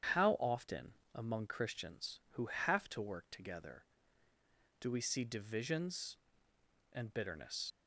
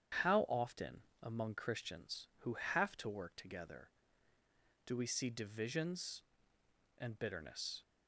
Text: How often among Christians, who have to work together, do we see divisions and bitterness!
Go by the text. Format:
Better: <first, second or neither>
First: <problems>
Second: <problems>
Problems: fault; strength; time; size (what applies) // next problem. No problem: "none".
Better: second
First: starts louder than the rest; strong; until 1.3 s; 8 dB // pauses between "often" and "among"; slight; at 0.9 s; 0.20 s long // leaves "bitterness" unfinished; at 7.7 s; 60 ms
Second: starts louder than the rest; strong; until 1.4 s; 8 dB // pauses between "often" and "among"; slight; at 1.0 s; 0.18 s long